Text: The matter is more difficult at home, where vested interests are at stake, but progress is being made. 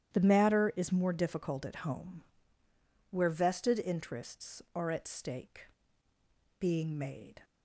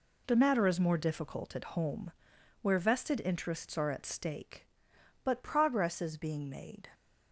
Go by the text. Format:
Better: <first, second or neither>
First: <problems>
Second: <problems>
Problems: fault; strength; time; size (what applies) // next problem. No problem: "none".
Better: second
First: starts louder than the rest; strong; until 1.1 s; 10.5 dB // skips "but progress is"; at 6.1 s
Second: none